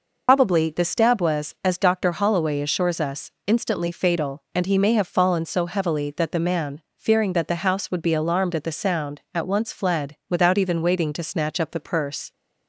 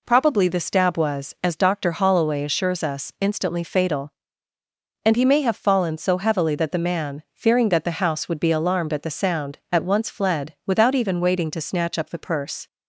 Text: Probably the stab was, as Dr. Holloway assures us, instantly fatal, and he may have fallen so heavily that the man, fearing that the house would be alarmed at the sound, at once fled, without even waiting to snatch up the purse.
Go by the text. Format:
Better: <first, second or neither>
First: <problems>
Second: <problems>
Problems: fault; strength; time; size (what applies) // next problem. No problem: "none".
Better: second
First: loses the start of "Probably"; at 0.2 s; 90 ms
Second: none